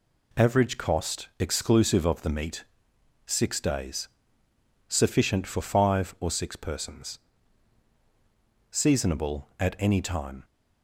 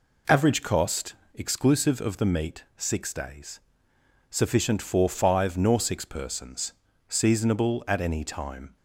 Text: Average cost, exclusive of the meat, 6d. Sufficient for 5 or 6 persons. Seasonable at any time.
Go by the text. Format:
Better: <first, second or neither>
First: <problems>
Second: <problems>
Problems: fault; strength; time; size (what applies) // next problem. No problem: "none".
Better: first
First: none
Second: says "nor" for "or"; at 5.5 s